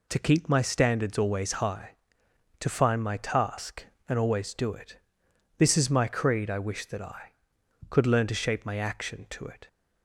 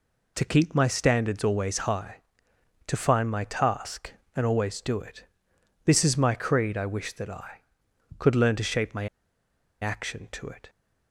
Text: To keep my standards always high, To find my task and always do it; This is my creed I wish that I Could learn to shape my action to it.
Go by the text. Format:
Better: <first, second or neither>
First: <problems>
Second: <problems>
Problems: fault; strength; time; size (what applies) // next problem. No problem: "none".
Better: first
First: none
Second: pauses between "my" and "action"; noticeable; at 9.0 s; 0.75 s long